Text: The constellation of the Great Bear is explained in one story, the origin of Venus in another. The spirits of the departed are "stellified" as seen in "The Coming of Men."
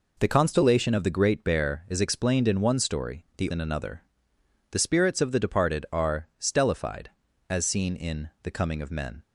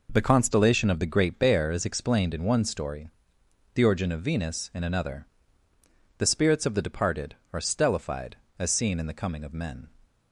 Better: second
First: skips "origin of Venus"; at 3.4 s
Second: none

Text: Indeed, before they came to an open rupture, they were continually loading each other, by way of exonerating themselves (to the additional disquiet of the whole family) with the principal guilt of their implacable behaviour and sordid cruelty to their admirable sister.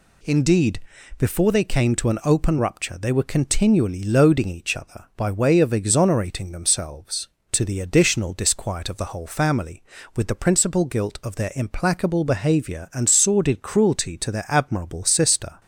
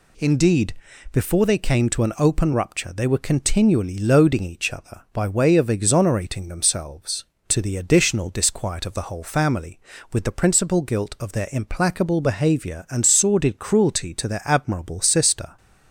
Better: neither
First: none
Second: none

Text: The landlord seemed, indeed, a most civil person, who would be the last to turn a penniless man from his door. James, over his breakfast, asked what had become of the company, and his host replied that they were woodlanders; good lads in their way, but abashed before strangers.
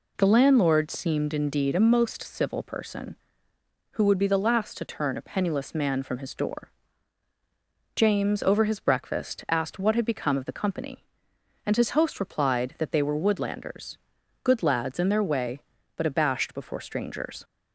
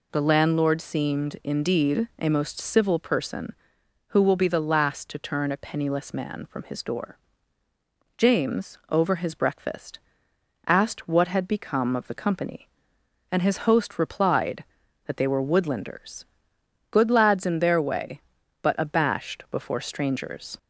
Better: first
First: none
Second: says "will" for "would"; at 4.2 s

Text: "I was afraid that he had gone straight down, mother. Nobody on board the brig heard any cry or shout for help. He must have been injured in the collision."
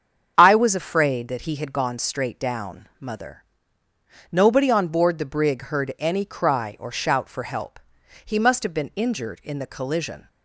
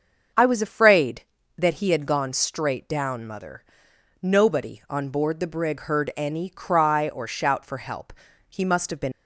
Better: first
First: starts louder than the rest; strong; until 1.3 s; 7.5 dB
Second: starts louder than the rest; until 1.6 s; 6.5 dB // stops before "injured in the collision"; at 9.1 s

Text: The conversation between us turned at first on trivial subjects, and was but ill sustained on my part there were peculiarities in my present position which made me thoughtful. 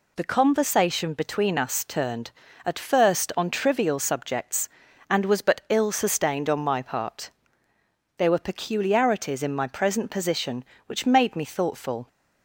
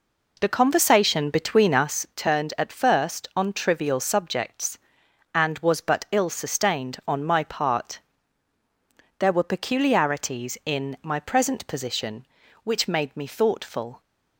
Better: first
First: pauses between "part" and "there"; noticeable; at 7.3 s; 0.86 s long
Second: starts louder than the rest; noticeable; until 2.1 s; 4 dB // pauses between "part" and "there"; at 7.9 s; 1.2 s long

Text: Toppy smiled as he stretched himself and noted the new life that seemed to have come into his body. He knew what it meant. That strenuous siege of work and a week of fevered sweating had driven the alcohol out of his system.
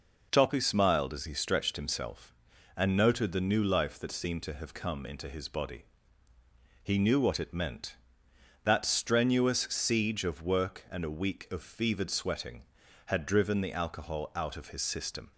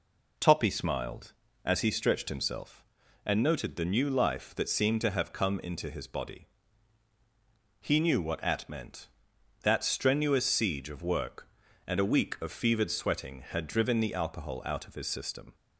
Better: first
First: none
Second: says "at" for "it"; at 8.4 s

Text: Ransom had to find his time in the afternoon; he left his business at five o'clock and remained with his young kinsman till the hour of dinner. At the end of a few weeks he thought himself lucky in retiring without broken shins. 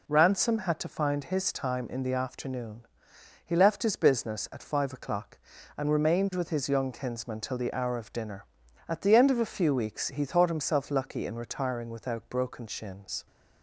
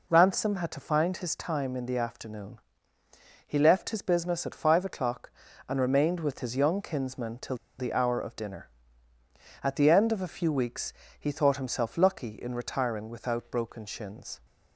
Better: first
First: none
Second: pauses between "till" and "the"; slight; at 7.5 s; 0.23 s long // pauses between "weeks" and "he"; slight; at 10.9 s; 0.28 s long

